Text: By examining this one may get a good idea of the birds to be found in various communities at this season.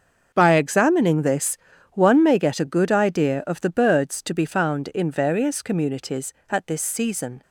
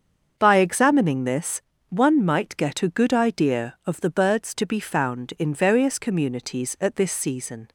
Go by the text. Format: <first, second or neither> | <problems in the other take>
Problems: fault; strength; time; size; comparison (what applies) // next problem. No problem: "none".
first | starts louder than the rest; until 1.3 s; 7 dB; also in the first // pauses between "this" and "one"; slight; at 1.6 s; 0.26 s long; slight in the first // says "might" for "may"; at 2.2 s